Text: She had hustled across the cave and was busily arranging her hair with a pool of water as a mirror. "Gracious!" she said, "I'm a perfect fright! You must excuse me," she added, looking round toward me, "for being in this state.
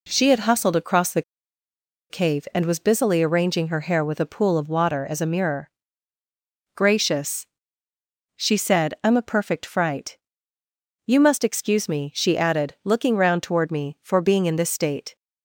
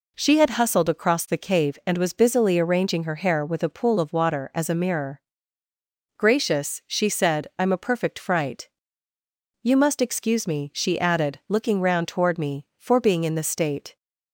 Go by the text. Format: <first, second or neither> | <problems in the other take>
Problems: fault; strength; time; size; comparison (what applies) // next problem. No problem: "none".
second | pauses between "the" and "cave"; noticeable; at 1.2 s; 0.88 s long